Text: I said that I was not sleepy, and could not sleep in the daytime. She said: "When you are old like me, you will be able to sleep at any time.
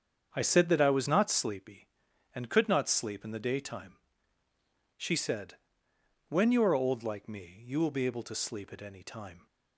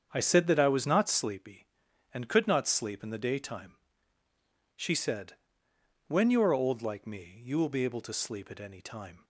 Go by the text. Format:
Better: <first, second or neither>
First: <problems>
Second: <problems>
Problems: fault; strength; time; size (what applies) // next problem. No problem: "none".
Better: neither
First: starts louder than the rest; strong; until 1.3 s; 7.5 dB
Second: starts louder than the rest; strong; until 1.1 s; 7.5 dB